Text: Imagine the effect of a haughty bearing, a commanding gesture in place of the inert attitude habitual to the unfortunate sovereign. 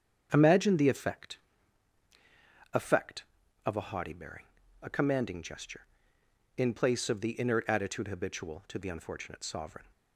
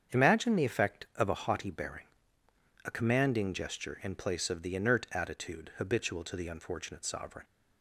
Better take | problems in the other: second | starts louder than the rest; strong; until 1.3 s; 8 dB; strong in the second // says "effect" twice; at 2.7 s

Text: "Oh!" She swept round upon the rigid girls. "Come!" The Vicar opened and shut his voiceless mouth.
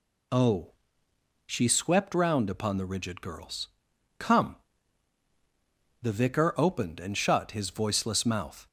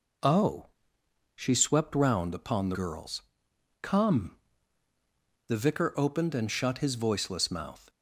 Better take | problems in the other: first | skips "rigid"; at 2.7 s

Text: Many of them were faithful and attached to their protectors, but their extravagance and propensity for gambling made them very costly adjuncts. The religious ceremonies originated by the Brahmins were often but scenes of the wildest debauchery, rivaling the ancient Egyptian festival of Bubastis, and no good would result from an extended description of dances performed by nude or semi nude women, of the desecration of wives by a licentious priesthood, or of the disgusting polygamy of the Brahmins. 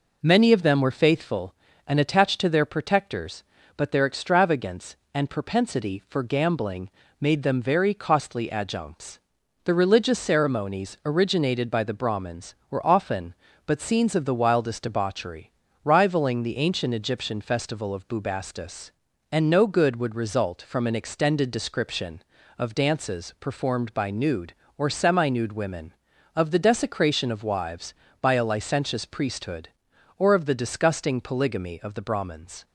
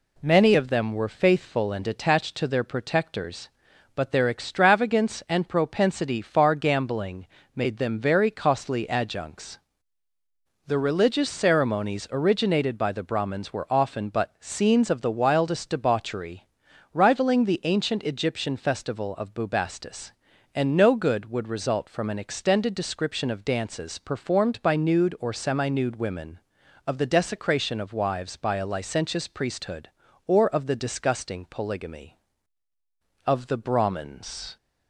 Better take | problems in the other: first | says "far" for "for"; at 6.2 s // pauses between "gambling" and "made"; slight; at 7.2 s; 0.28 s long; slight in the first

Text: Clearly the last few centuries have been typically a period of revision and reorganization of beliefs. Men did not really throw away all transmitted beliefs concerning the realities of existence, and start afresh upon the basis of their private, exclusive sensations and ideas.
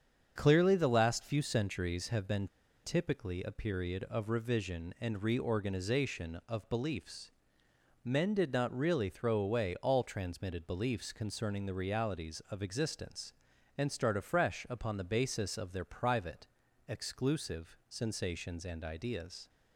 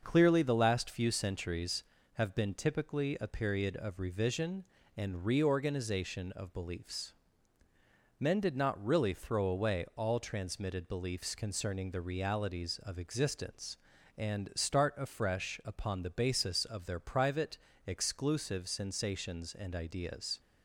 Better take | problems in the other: second | starts louder than the rest; strong; until 1.3 s; 7 dB; also in the second // pauses between "been" and "typically"; at 2.4 s; 0.36 s long

